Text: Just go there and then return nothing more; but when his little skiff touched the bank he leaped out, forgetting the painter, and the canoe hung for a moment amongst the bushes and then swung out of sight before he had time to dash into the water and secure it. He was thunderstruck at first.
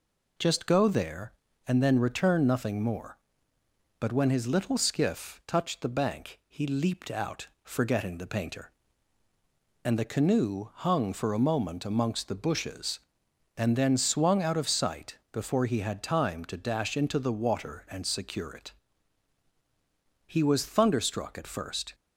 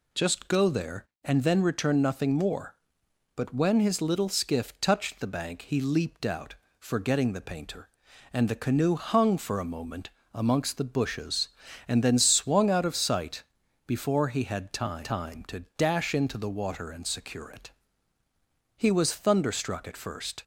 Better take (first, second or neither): first